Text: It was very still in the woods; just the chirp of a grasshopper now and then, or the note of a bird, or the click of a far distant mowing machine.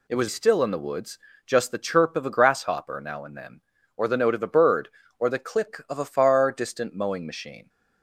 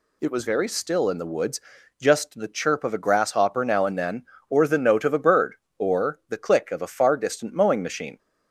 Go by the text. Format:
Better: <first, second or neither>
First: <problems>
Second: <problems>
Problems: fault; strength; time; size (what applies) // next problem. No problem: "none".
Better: second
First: skips "very"; at 0.2 s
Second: none